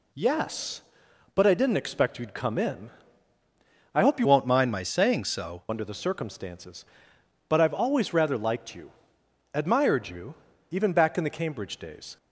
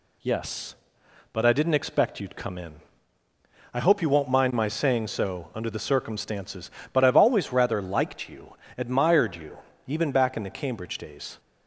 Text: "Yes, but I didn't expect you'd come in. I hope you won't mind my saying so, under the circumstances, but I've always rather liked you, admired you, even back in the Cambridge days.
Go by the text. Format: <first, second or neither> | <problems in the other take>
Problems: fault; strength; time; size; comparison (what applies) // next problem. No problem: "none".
second | changes voice from "won't" to "so"; from 4.2 to 5.6 s; 1.4 s long